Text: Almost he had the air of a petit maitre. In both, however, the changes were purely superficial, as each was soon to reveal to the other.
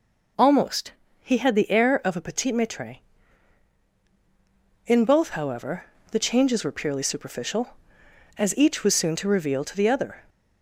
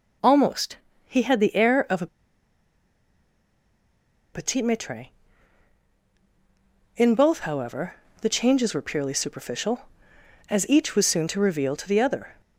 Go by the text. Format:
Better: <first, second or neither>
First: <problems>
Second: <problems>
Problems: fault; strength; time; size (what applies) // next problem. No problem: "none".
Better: first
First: pauses between "Almost" and "he"; slight; at 0.9 s; 0.28 s long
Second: pauses between "Almost" and "he"; slight; at 0.7 s; 0.28 s long // pauses between "a" and "petit"; strong; at 2.0 s; 2.2 s long